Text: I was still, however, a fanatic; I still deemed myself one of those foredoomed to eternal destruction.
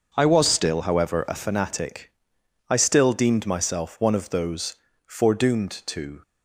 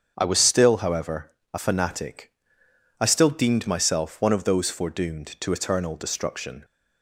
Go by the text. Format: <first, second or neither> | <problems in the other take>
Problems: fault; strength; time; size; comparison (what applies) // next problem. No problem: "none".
second | starts louder than the rest; noticeable; until 1.1 s; 6 dB; strong in the second // pauses between "those" and "foredoomed"; slight; at 4.7 s; 0.32 s long // stops before "eternal destruction"; at 6.2 s